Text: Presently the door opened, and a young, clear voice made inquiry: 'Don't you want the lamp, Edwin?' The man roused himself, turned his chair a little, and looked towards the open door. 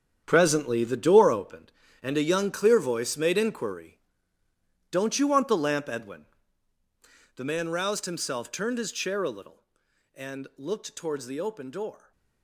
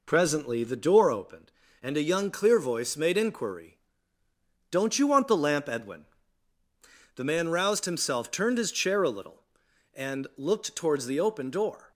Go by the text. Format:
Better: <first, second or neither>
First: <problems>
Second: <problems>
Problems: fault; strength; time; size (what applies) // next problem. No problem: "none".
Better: second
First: gets quieter; strong; throughout; 11.5 dB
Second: none